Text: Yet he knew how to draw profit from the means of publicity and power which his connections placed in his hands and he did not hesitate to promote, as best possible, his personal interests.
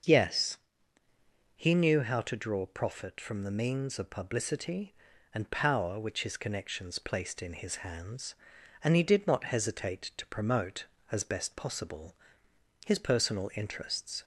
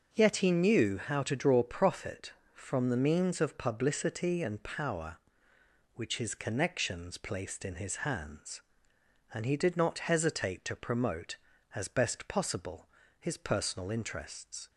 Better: second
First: starts louder than the rest; until 2.0 s; 6.5 dB // says "Yes" for "Yet"; at 0.0 s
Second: starts louder than the rest; until 1.1 s; 6 dB

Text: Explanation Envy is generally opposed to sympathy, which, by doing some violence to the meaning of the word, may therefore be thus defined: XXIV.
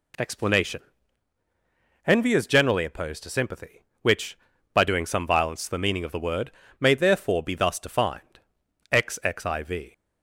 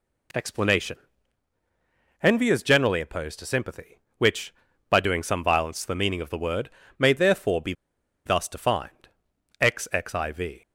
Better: first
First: pauses between "Explanation" and "Envy"; strong; at 0.8 s; 1.2 s long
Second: pauses between "Explanation" and "Envy"; strong; at 0.9 s; 1.2 s long // pauses between "be" and "thus"; noticeable; at 7.7 s; 0.52 s long

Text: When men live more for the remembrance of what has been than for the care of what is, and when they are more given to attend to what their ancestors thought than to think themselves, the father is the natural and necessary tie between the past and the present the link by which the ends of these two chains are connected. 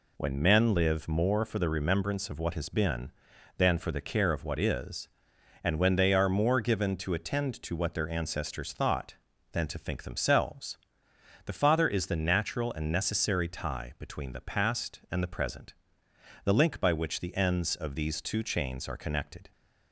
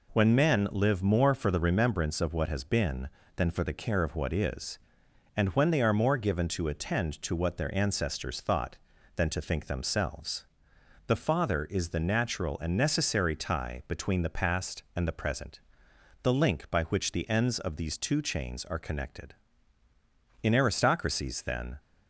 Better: first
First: pauses between "present" and "the"; noticeable; at 15.7 s; 0.70 s long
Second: pauses between "present" and "the"; noticeable; at 15.5 s; 0.62 s long // goes on to say "In aristocracies then"; from 20.4 s on; 1.3 s long

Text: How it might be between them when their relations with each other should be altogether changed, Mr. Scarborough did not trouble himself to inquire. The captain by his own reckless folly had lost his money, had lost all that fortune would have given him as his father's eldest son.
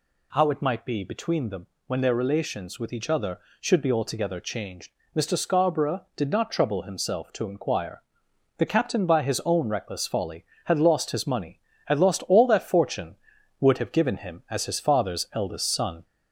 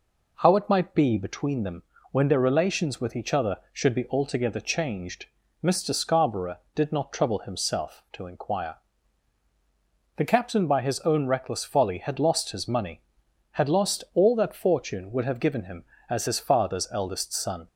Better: second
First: gets louder; slight; throughout; 2.5 dB // pauses between "them" and "when"; slight; at 1.6 s; 0.20 s long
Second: pauses between "them" and "when"; slight; at 1.8 s; 0.28 s long

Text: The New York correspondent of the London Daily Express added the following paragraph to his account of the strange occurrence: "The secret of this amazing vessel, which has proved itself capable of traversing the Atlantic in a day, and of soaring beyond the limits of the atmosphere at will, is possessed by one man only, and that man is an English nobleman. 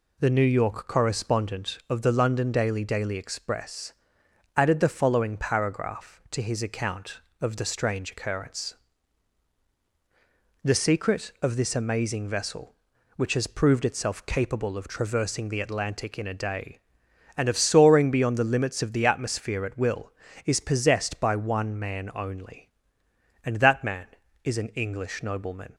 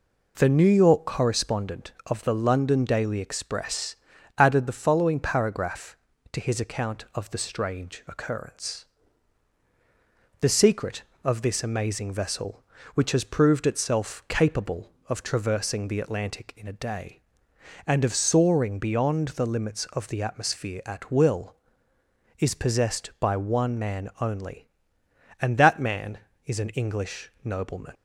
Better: second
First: says "Daily" twice; at 2.8 s // pauses between "Express" and "added"; noticeable; at 3.9 s; 0.64 s long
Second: pauses between "Express" and "added"; at 3.9 s; 0.42 s long

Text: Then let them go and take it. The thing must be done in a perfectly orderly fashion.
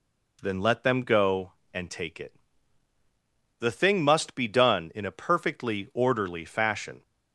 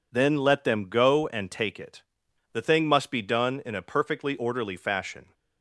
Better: neither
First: none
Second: none

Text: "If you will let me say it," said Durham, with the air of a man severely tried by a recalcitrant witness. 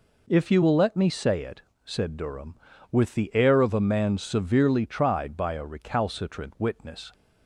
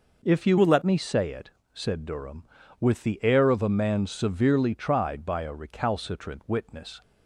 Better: first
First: none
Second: changes voice from "will" to "let"; from 0.5 to 0.8 s; 0.3 s long

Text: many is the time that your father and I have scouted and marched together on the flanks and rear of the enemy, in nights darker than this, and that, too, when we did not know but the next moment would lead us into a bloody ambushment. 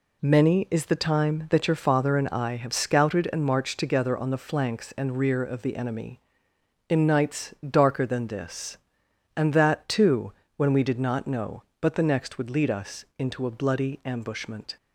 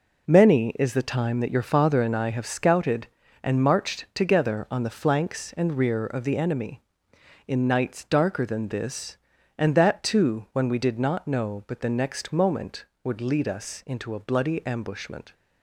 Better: second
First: skips "moment"; at 12.3 s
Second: none

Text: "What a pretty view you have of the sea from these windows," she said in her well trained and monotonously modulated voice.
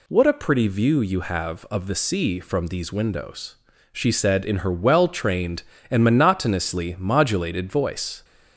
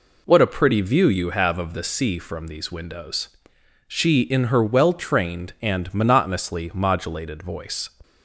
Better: first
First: none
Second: skips "said"; at 4.2 s

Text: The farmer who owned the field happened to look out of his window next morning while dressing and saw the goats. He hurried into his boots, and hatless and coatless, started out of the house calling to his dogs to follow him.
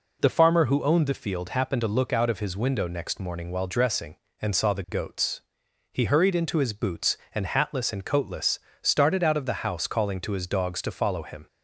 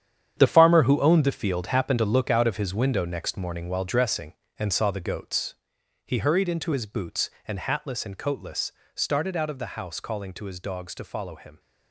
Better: first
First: none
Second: gets quieter; strong; throughout; 11 dB

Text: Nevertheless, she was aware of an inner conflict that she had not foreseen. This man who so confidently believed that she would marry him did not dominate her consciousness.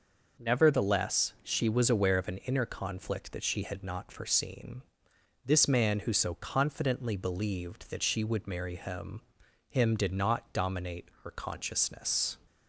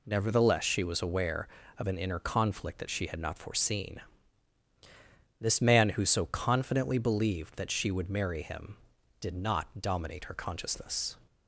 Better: second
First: says "him" twice; at 9.6 s // pauses between "dominate" and "her"; slight; at 11.0 s; 0.18 s long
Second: none

